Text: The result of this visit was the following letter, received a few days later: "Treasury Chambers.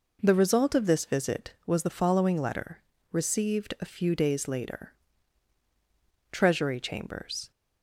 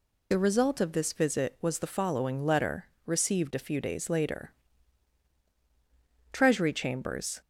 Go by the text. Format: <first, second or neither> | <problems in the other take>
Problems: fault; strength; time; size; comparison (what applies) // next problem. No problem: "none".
first | loses the start of "The"; at 0.3 s; 55 ms